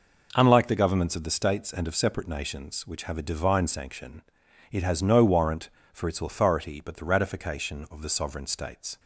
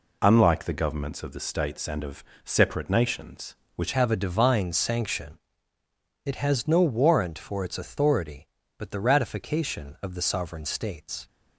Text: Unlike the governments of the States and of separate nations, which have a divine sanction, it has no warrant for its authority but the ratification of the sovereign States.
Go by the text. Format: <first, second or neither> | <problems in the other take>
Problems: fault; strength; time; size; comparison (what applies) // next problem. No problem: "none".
first | pauses between "of" and "separate"; slight; at 2.2 s; 0.20 s long // changes voice at "have"; from 3.9 s on; 7.3 s long